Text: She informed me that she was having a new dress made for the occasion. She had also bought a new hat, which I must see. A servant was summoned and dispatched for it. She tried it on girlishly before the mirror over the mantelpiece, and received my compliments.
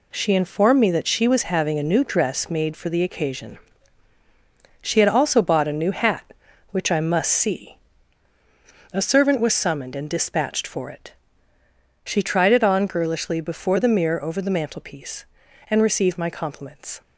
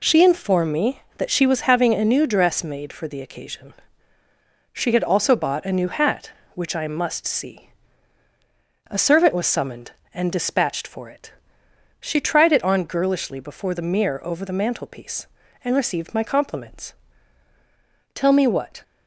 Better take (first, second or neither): first